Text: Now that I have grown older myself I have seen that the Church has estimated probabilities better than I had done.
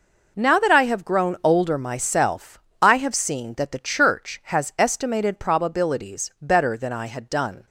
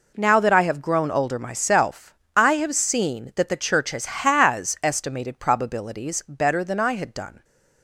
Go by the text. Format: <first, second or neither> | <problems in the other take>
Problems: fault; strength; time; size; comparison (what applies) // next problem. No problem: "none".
first | pauses between "myself" and "I"; slight; at 2.1 s; 0.22 s long; slight in the first // says "has" twice; at 4.0 s